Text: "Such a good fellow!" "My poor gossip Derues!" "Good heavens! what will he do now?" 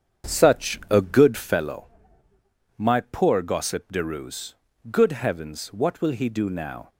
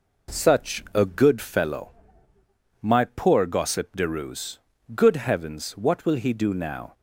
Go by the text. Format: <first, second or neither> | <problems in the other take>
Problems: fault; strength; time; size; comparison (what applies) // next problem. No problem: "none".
second | starts louder than the rest; strong; until 1.6 s; 8 dB